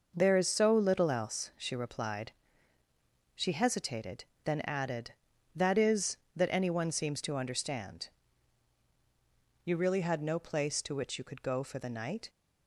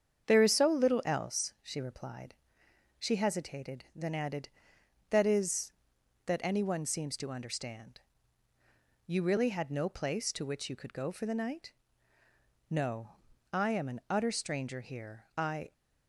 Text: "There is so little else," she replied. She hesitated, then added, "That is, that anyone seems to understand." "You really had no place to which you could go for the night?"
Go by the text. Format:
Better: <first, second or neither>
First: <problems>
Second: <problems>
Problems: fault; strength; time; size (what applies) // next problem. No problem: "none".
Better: first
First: none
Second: starts louder than the rest; strong; until 1.2 s; 7.5 dB // goes on to say "No I am an utter stranger here I"; strong; from 12.6 s on; 3.0 s long